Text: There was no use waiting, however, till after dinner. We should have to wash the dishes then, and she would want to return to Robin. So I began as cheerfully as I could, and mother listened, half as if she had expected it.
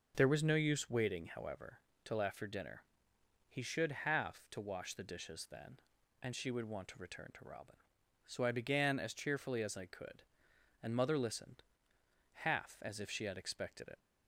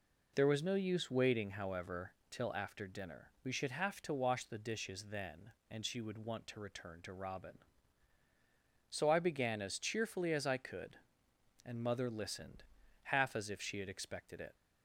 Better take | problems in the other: second | says "He" for "We"; at 3.4 s

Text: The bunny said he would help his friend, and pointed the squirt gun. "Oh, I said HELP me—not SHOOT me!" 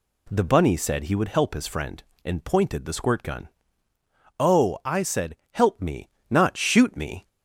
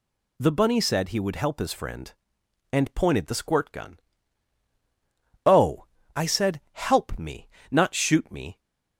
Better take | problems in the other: neither | none

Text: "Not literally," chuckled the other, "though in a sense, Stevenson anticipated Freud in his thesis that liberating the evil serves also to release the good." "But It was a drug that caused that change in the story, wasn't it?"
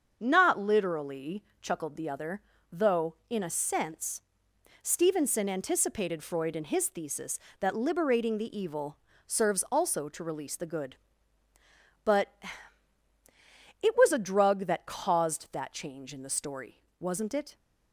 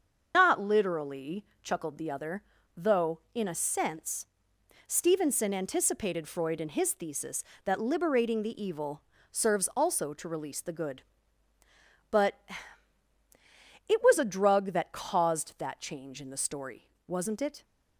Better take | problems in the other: first | loses the start of "Not"; at 0.3 s; 145 ms // starts louder than the rest; until 1.3 s; 6.5 dB; also in the first // pauses between "evil" and "serves"; slight; at 9.0 s; 0.30 s long; slight in the first // pauses between "But" and "It"; strong; at 12.3 s; 1.5 s long; strong in the first

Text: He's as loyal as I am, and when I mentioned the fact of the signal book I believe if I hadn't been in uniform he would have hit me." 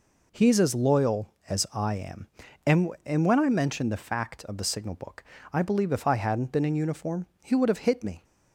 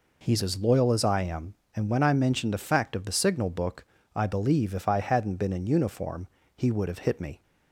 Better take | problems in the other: second | says "and" twice; at 3.0 s // pauses between "book" and "I"; slight; at 5.2 s; 0.28 s long; slight in the second // pauses between "uniform" and "he"; slight; at 7.2 s; 0.18 s long; slight in the second

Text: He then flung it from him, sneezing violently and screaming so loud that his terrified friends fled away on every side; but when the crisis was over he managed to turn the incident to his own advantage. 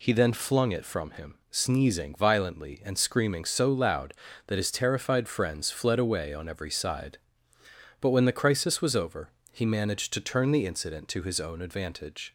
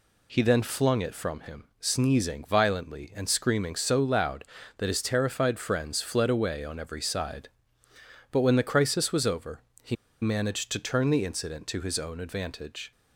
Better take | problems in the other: first | pauses between "over" and "he"; slight; at 9.5 s; 0.24 s long; slight in the first // pauses between "he" and "managed"; slight; at 9.9 s; 0.27 s long

